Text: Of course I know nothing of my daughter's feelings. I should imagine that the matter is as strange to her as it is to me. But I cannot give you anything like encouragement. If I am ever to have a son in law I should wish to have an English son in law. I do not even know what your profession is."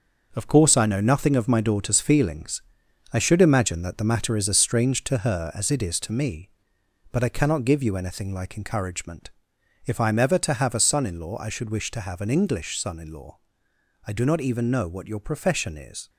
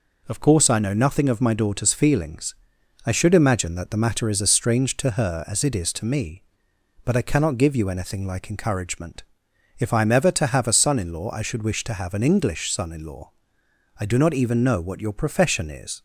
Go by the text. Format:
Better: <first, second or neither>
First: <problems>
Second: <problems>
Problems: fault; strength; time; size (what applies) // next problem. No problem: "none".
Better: second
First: gets quieter; strong; throughout; 8 dB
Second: none